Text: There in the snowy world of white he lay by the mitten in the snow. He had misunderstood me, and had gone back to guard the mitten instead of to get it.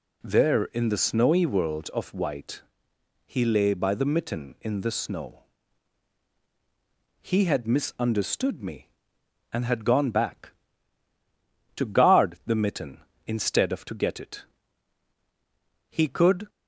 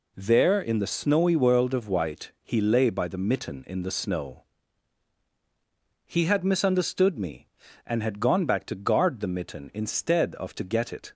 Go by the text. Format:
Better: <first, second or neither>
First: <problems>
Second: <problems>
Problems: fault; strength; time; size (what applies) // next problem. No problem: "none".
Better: second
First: pauses between "white" and "he"; noticeable; at 2.6 s; 0.62 s long // goes on to say "He could"; from 15.8 s on; 0.60 s long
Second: none